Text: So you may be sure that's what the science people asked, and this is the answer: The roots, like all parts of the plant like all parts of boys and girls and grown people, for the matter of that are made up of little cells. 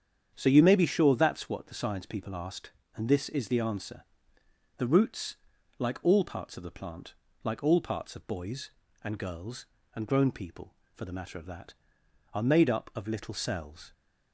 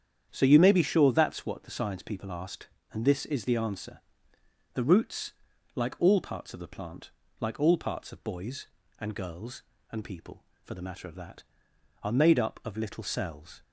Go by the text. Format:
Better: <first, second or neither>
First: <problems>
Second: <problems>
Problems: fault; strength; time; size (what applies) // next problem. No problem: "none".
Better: first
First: starts louder than the rest; strong; until 1.3 s; 8 dB // pauses between "plant" and "like"; slight; at 7.1 s; 0.32 s long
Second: starts louder than the rest; strong; until 1.3 s; 8.5 dB // pauses between "plant" and "like"; slight; at 7.0 s; 0.32 s long // skips "grown"; at 10.0 s